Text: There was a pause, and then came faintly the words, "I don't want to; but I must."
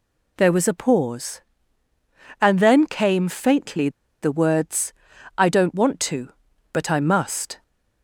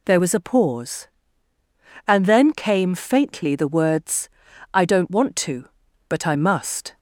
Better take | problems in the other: second | pauses between "faintly" and "the"; slight; at 3.8 s; 0.32 s long

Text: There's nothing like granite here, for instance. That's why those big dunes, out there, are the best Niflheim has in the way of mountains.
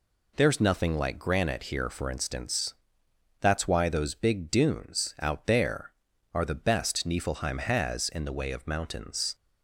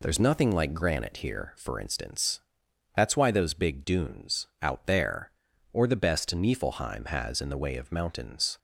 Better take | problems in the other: first | says "or" for "are"; at 5.7 s

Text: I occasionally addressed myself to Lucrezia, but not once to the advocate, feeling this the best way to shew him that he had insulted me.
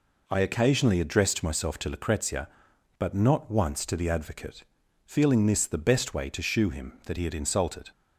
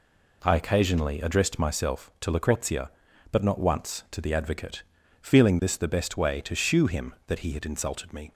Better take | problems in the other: second | stops before "me"; at 7.9 s

